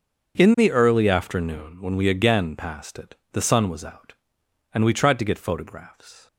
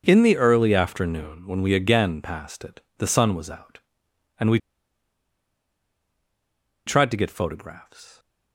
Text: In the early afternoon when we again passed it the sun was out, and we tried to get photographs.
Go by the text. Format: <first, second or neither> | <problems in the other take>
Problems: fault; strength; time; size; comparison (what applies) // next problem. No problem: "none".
first | starts louder than the rest; until 1.0 s; 6.5 dB; also in the first // pauses between "it" and "the"; slight; at 2.8 s; 0.18 s long; slight in the first // pauses between "we" and "tried"; strong; at 4.5 s; 2.2 s long